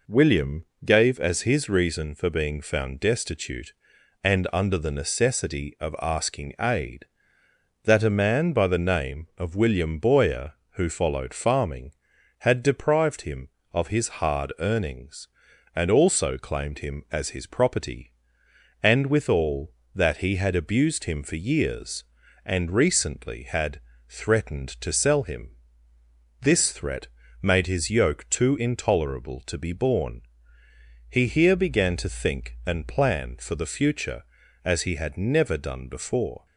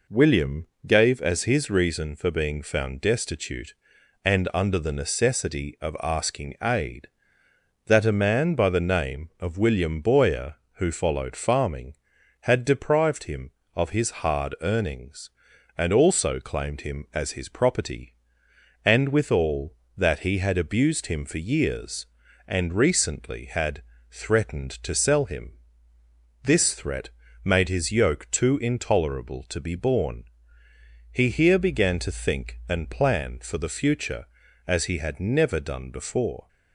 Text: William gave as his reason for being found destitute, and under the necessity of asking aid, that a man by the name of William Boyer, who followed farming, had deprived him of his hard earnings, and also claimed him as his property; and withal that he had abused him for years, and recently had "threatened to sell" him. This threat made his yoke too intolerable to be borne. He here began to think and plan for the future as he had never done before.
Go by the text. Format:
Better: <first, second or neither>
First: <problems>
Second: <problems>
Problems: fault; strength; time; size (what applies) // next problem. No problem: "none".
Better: neither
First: pauses between "William" and "gave"; slight; at 0.6 s; 0.18 s long // pauses between "had" and "threatened"; slight; at 23.8 s; 0.28 s long // pauses between "threat" and "made"; slight; at 27.0 s; 0.34 s long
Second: pauses between "William" and "gave"; slight; at 0.6 s; 0.18 s long // pauses between "had" and "threatened"; slight; at 23.8 s; 0.28 s long // pauses between "threat" and "made"; slight; at 27.0 s; 0.34 s long